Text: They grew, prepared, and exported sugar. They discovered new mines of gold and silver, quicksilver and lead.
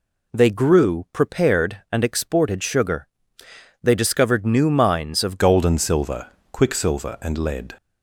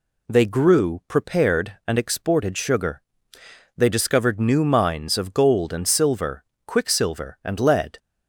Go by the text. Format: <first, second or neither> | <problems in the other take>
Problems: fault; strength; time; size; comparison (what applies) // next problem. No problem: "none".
second | changes voice at "gold"; from 5.3 s on; 2.4 s long